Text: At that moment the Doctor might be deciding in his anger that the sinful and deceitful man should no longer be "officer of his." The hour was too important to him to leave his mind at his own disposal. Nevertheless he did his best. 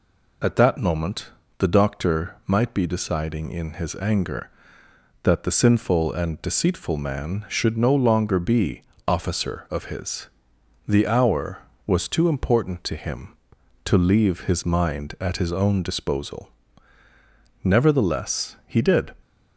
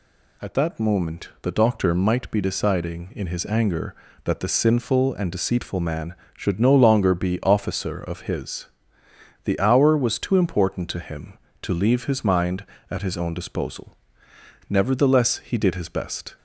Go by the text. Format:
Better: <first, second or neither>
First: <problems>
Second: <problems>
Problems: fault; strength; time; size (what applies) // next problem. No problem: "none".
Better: second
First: pauses between "moment" and "the"; slight; at 1.3 s; 0.26 s long // pauses between "be" and "officer"; slight; at 8.8 s; 0.22 s long // stops before "his best"; at 19.2 s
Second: none